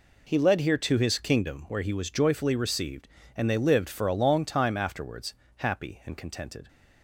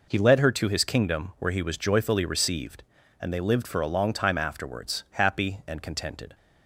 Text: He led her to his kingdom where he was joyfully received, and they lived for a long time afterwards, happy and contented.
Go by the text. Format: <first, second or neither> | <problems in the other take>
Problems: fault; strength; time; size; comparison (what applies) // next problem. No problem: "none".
second | says "here" for "her"; at 0.5 s